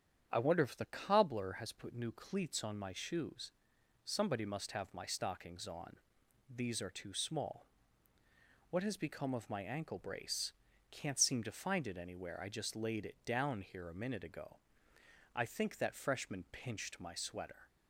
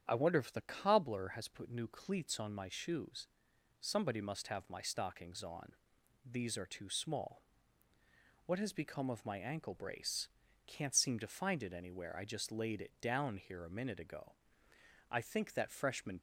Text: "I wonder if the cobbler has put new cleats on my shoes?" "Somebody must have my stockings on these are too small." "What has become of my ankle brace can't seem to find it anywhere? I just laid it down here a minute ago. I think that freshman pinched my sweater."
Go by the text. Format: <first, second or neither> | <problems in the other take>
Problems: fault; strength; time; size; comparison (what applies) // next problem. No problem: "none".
first | starts louder than the rest; strong; until 1.0 s; 9 dB; strong in the first // pauses between "on" and "these"; noticeable; at 5.7 s; 0.50 s long; noticeable in the first // pauses between "brace" and "can't"; at 10.2 s; 0.40 s long; also in the first // stops before "pinched my sweater"; at 16.1 s